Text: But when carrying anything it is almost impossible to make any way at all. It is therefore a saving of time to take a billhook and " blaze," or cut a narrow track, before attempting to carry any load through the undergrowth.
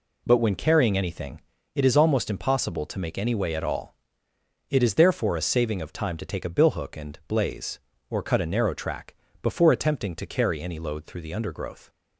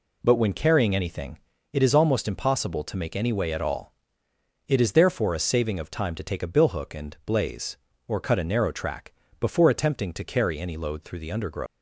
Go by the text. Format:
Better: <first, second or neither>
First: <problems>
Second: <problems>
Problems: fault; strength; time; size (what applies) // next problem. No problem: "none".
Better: first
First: pauses between "anything" and "it"; slight; at 1.4 s; 0.34 s long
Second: pauses between "anything" and "it"; slight; at 1.3 s; 0.34 s long // leaves "undergrowth" unfinished; at 11.6 s; 205 ms